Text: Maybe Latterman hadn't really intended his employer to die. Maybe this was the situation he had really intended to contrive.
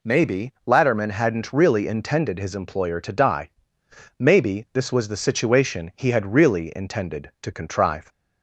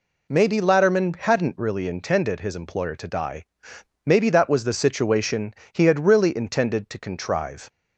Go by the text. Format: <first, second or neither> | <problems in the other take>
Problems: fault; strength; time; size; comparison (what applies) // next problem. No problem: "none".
first | says "that" for "this"; at 4.2 s // pauses between "situation" and "he"; slight; at 5.5 s; 0.20 s long